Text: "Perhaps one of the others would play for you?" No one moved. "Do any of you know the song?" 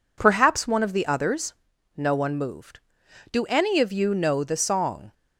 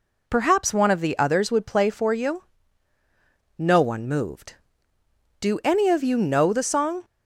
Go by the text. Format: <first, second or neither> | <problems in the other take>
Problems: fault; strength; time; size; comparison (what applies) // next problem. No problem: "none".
second | skips "would play for you"; at 1.7 s